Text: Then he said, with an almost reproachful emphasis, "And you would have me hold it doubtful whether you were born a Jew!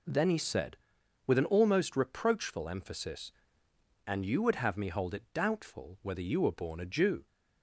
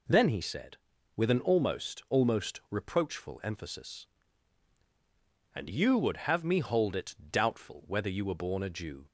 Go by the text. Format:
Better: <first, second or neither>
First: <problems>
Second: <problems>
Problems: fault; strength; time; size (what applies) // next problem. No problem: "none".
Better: first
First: none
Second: says "almost" twice; at 2.0 s // pauses between "it" and "doubtful"; slight; at 7.1 s; 0.16 s long